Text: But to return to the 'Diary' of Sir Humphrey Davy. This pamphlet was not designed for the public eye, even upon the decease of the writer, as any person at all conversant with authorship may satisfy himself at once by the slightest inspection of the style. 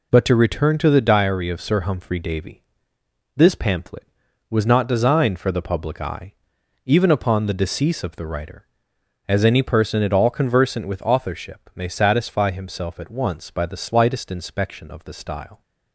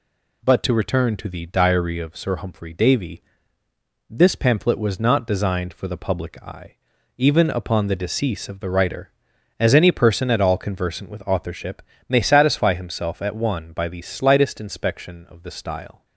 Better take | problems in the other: first | pauses between "authorship" and "may"; slight; at 11.8 s; 0.26 s long // says "one" for "once"; at 13.3 s

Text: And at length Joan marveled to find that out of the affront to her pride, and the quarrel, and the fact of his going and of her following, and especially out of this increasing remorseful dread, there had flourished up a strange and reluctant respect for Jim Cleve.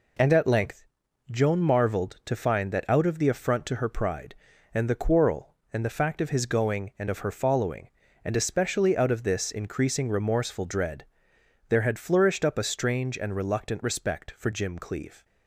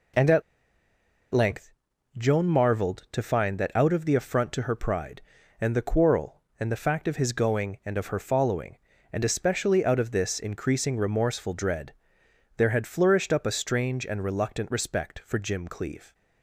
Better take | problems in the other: first | pauses between "at" and "length"; noticeable; at 0.4 s; 0.91 s long // pauses between "length" and "Joan"; noticeable; at 1.7 s; 0.46 s long; noticeable in the first

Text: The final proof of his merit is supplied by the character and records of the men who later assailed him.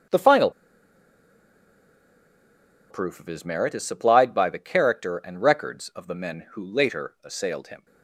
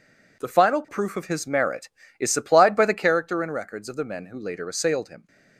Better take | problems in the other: second | starts louder than the rest; strong; until 3.5 s; 8 dB // pauses between "final" and "proof"; strong; at 0.4 s; 2.4 s long

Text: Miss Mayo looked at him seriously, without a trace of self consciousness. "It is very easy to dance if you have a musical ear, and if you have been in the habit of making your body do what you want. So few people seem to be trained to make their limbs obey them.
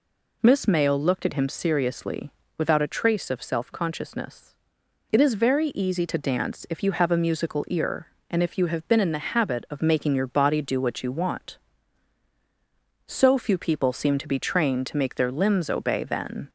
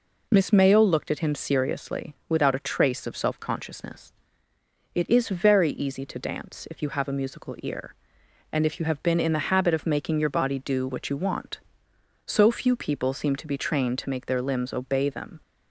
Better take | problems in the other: second | says "then" for "them"; at 16.0 s

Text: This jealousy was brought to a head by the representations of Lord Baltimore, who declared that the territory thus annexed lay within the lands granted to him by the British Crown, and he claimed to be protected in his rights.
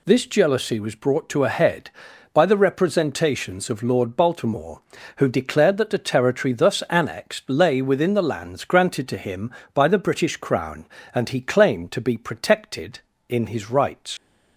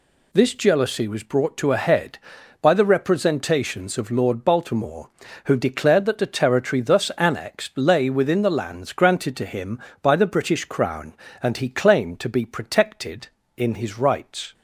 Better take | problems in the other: second | leaves "rights" unfinished; at 14.1 s; 85 ms

